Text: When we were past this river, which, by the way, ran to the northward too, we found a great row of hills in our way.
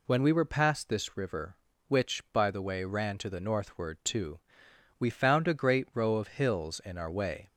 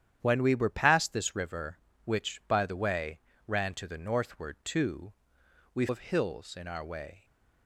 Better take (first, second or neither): first